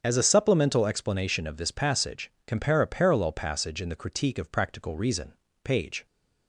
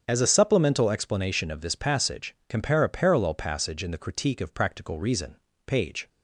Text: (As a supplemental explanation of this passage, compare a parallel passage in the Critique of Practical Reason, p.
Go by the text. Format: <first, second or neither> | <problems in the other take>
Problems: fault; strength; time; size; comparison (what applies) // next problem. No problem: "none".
neither | starts louder than the rest; strong; the same in both